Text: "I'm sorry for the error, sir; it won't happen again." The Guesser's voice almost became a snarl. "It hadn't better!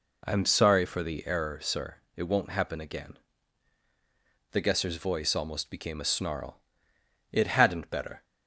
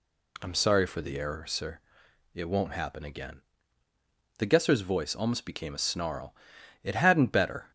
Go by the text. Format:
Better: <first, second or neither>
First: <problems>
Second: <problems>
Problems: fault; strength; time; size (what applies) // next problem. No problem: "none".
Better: neither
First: none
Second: none